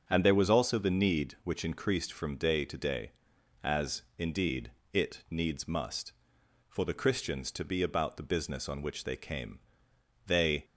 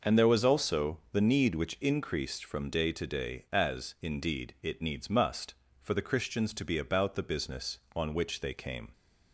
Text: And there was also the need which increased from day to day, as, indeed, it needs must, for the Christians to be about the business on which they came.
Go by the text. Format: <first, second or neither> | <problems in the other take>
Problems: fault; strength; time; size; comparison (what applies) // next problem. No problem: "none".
second | starts louder than the rest; until 1.0 s; 7 dB // goes on to say "They"; slight; from 10.2 s on; 0.38 s long